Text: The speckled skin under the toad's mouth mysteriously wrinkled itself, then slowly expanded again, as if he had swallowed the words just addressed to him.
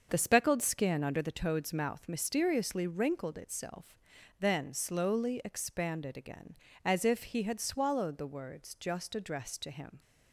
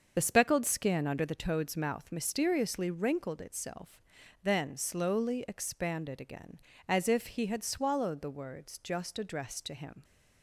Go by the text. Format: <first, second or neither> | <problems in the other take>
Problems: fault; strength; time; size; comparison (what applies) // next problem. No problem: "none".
first | loses the start of "The"; at 0.1 s; 40 ms // starts louder than the rest; until 1.1 s; 6.5 dB; also in the first